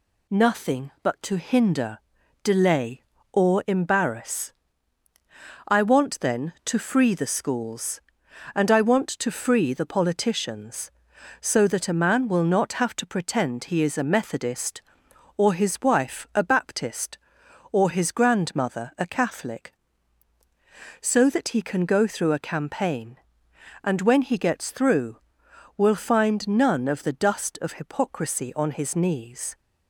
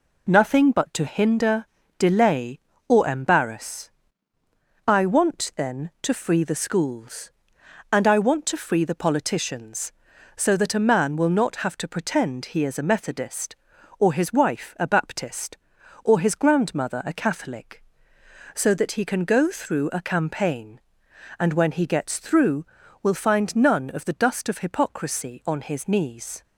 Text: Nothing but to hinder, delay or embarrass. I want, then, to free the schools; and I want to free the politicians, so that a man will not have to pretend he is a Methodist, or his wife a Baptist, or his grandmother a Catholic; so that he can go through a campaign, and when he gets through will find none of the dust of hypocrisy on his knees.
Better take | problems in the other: neither | none

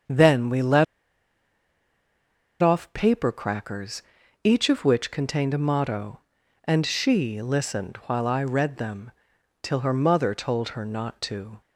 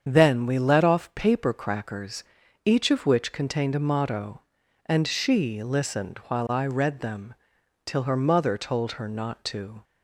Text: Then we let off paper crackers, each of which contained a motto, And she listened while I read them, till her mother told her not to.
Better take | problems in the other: second | starts louder than the rest; strong; until 2.8 s; 7.5 dB; strong in the second // pauses between "let" and "off"; strong; at 0.8 s; 1.7 s long

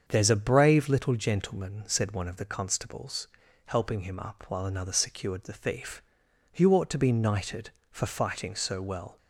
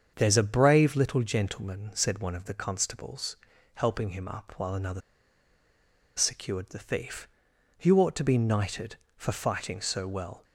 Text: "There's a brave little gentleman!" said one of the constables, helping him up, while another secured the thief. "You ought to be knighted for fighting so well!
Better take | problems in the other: first | starts louder than the rest; strong; until 1.1 s; 7 dB; strong in the first // pauses between "another" and "secured"; at 5.0 s; 1.1 s long

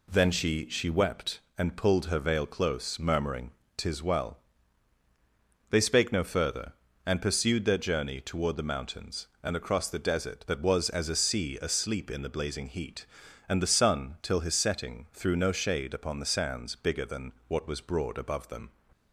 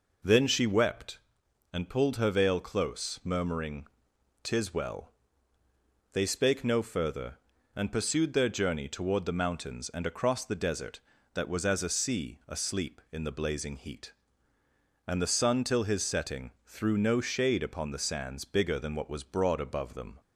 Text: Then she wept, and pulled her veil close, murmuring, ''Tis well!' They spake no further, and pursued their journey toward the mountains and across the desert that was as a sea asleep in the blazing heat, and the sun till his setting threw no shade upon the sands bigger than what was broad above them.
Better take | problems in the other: second | says "she" twice; at 0.6 s // pauses between "than" and "what"; slight; at 17.3 s; 0.16 s long

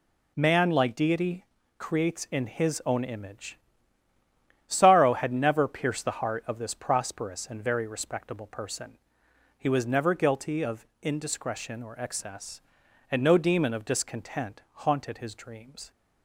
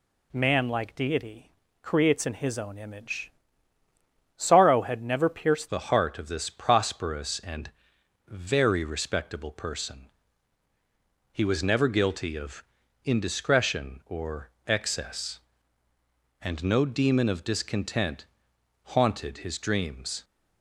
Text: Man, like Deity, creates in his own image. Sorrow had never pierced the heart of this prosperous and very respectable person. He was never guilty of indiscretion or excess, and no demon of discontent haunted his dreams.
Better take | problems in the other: first | changes voice at "the"; from 5.6 s on; 14.6 s long // pauses between "and" and "very"; noticeable; at 7.6 s; 0.58 s long // pauses between "of" and "indiscretion"; at 12.6 s; 0.40 s long; slight in the first // pauses between "or" and "excess"; slight; at 14.4 s; 0.18 s long // pauses between "discontent" and "haunted"; noticeable; at 18.2 s; 0.60 s long

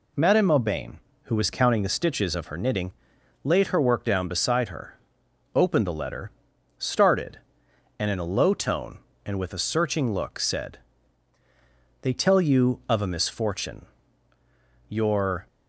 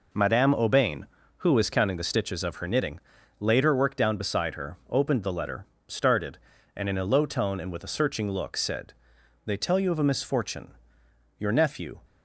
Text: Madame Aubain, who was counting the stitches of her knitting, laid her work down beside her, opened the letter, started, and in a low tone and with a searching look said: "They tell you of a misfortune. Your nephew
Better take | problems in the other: second | stops before "nephew"; at 15.4 s

